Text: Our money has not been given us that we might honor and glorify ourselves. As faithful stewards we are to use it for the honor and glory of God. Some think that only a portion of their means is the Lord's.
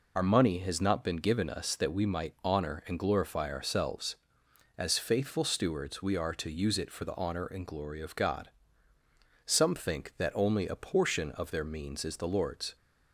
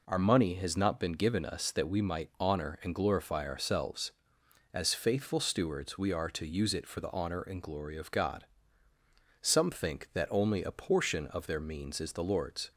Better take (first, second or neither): second